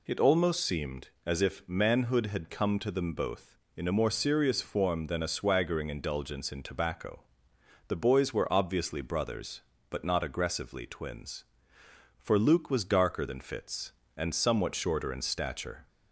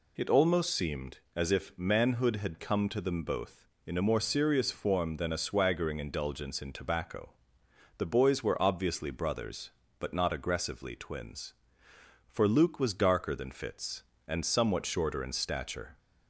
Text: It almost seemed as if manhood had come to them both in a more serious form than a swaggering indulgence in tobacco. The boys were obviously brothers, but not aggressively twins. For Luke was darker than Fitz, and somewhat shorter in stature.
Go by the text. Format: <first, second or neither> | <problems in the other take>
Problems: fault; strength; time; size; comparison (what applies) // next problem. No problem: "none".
neither | none